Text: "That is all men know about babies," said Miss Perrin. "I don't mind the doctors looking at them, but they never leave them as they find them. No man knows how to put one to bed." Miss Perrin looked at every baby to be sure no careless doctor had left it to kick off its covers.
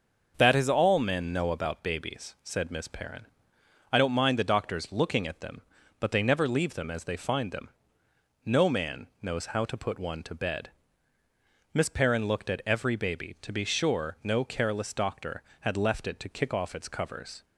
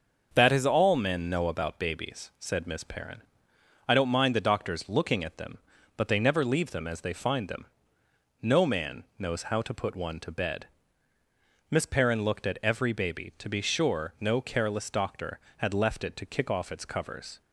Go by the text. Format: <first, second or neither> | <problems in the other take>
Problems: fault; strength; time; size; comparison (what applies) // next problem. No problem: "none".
neither | starts louder than the rest; the same in both // pauses between "man" and "knows"; slight; the same in both